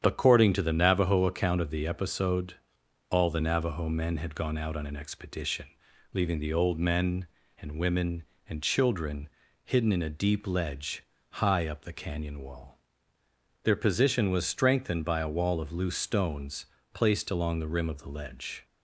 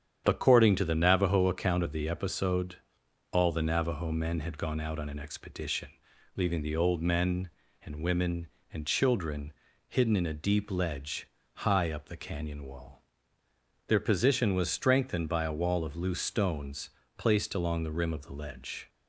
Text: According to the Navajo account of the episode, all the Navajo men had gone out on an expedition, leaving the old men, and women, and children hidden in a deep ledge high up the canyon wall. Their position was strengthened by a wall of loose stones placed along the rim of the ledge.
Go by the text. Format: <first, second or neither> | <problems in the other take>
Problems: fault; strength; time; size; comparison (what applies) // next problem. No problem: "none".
neither | starts louder than the rest; strong; the same in both // pauses between "children" and "hidden"; slight; the same in both // pauses between "ledge" and "high"; slight; the same in both // pauses between "stones" and "placed"; slight; the same in both